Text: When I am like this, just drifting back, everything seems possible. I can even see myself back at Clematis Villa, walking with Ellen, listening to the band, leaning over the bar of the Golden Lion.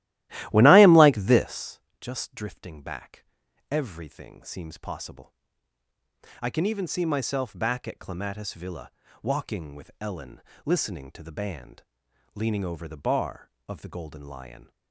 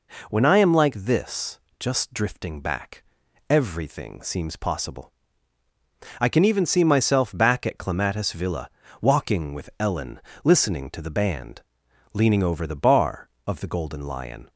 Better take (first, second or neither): second